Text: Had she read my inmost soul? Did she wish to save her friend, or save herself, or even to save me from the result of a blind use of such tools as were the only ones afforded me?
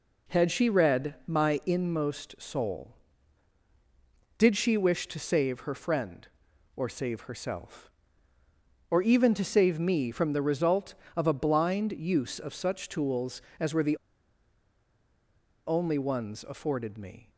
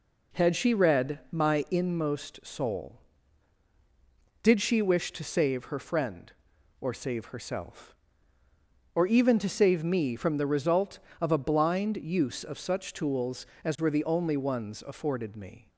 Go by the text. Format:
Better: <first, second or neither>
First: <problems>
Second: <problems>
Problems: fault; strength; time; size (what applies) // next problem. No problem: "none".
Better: second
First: pauses between "the" and "only"; strong; at 13.9 s; 1.7 s long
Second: none